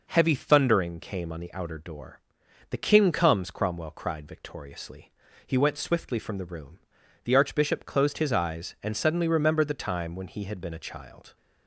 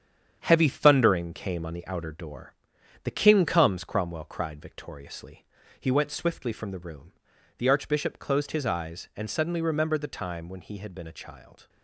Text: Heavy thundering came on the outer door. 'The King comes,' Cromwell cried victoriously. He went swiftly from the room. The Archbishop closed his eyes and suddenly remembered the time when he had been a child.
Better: first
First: none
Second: gets quieter; throughout; 6 dB

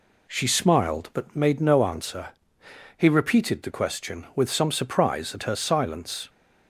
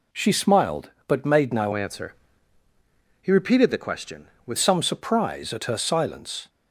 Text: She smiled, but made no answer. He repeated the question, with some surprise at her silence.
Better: first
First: none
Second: changes voice from "answer" to "with"; from 1.7 to 4.5 s; 2.8 s long

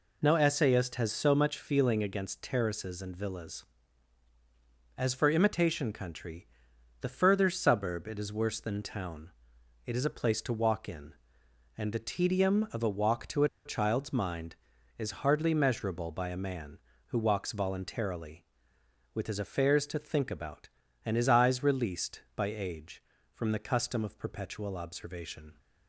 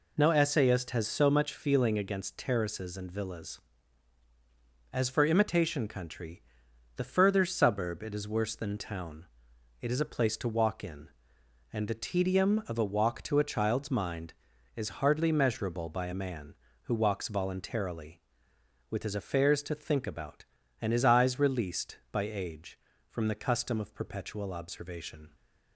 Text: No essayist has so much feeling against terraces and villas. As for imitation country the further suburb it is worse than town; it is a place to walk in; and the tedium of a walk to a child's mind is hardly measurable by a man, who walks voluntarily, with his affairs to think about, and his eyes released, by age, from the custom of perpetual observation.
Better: second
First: pauses between "country" and "the"; noticeable; at 6.4 s; 0.54 s long // pauses between "a" and "child's"; slight; at 13.4 s; 0.17 s long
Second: pauses between "country" and "the"; noticeable; at 6.4 s; 0.54 s long

